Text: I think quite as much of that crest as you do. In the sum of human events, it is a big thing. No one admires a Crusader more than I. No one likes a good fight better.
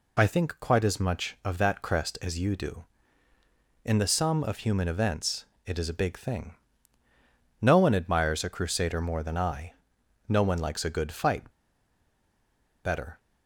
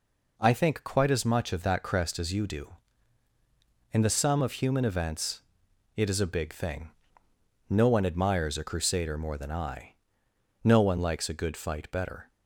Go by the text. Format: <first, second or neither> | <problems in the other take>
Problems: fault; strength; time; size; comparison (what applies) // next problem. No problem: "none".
second | pauses between "fight" and "better"; strong; at 11.5 s; 1.3 s long